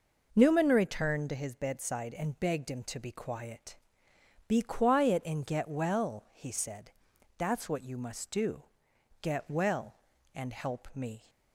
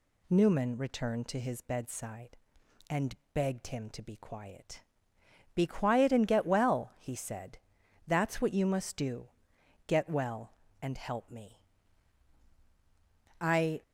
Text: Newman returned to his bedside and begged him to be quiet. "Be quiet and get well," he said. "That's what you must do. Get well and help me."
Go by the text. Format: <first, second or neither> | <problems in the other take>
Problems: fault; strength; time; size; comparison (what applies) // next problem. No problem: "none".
first | pauses between "and" and "begged"; slight; at 3.1 s; 0.18 s long // goes on to say "I"; slight; from 13.3 s on; 0.42 s long